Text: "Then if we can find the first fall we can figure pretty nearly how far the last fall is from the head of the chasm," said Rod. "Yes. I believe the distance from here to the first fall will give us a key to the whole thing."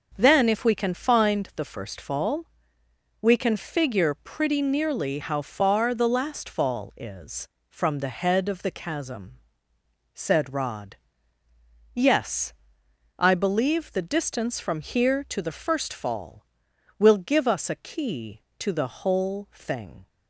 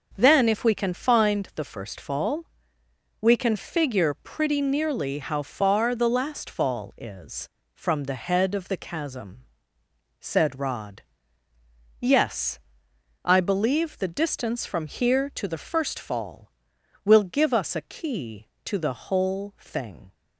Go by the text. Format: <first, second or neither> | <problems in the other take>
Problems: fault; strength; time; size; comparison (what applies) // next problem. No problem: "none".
neither | starts louder than the rest; the same in both // pauses between "fall" and "we"; noticeable; the same in both